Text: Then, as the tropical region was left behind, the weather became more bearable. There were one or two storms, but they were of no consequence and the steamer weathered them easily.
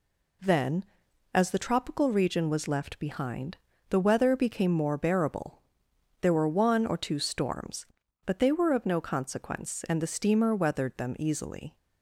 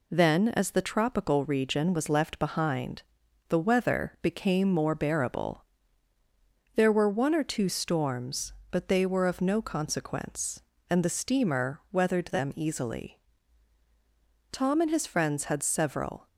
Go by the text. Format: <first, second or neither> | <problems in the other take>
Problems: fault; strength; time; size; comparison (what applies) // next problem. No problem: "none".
first | goes on to say "Tom and his friends had several"; strong; from 14.5 s on; 1.7 s long